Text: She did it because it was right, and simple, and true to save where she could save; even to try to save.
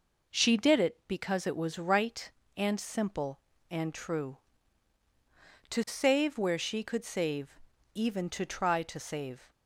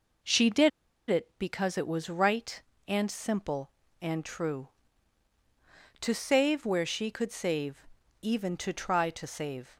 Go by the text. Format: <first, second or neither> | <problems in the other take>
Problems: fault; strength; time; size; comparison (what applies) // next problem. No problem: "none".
first | pauses between "did" and "it"; at 0.6 s; 0.39 s long